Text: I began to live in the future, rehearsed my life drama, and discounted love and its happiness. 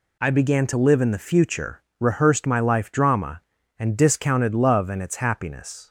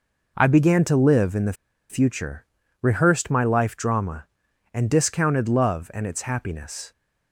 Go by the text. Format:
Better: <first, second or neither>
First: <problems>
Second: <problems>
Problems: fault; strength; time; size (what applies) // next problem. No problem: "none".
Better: first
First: none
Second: pauses between "the" and "future"; slight; at 1.5 s; 0.36 s long